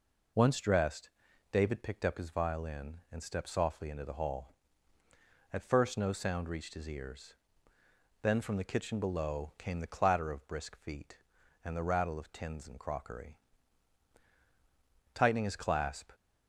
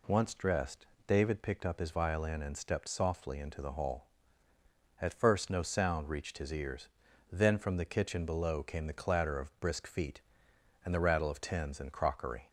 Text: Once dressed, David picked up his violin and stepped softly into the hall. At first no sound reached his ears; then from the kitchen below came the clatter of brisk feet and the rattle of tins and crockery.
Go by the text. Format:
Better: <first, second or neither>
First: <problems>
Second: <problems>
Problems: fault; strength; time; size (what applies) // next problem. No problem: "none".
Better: second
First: goes on to say "Tightening his clasp"; noticeable; from 15.1 s on; 0.96 s long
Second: none